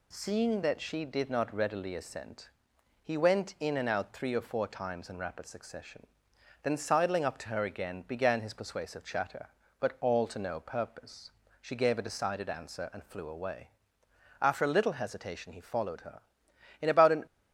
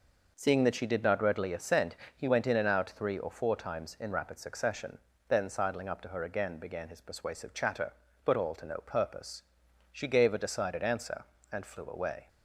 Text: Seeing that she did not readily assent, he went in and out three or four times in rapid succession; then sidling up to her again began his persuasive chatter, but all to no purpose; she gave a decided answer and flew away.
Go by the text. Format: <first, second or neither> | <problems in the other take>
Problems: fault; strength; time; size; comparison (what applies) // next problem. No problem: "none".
second | goes on to say "After a little hesitation he followed her In about an"; strong; from 14.4 s on; 2.8 s long